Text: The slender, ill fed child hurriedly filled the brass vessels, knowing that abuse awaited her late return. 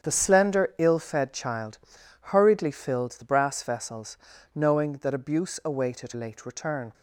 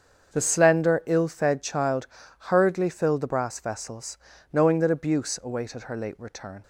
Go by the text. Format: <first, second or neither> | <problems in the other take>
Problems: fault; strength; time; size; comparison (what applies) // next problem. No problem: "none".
second | starts louder than the rest; strong; until 1.0 s; 8 dB; also in the second // pauses between "child" and "hurriedly"; noticeable; at 1.7 s; 0.50 s long; also in the second // skips "her"; at 6.1 s